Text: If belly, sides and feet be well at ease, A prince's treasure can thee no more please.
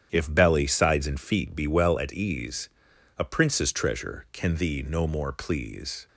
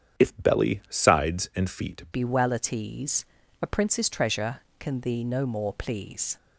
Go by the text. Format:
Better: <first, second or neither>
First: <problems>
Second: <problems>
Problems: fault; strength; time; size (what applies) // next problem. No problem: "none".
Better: first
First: starts louder than the rest; strong; until 1.1 s; 9.5 dB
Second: starts louder than the rest; strong; until 1.3 s; 8.5 dB // changes voice at "be"; from 2.1 s on; 4.2 s long